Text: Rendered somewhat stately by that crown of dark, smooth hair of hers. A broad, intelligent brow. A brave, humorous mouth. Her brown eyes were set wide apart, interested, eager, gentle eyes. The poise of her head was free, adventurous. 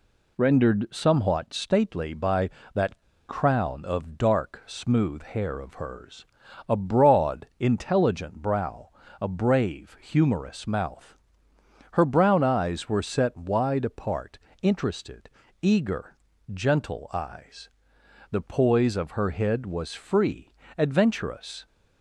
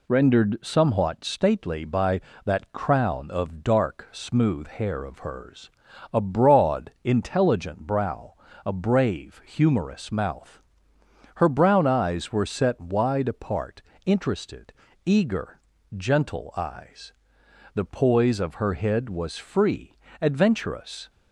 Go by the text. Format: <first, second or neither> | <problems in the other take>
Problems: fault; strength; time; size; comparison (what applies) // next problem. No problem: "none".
second | pauses between "that" and "crown"; slight; at 2.9 s; 0.30 s long